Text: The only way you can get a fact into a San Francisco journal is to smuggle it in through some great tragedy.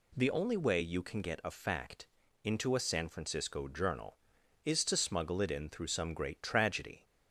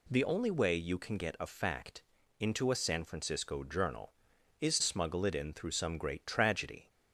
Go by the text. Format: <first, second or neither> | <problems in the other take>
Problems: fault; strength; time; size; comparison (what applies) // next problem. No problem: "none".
first | pauses between "fact" and "into"; at 2.0 s; 0.38 s long; also in the first // skips "to"; at 4.8 s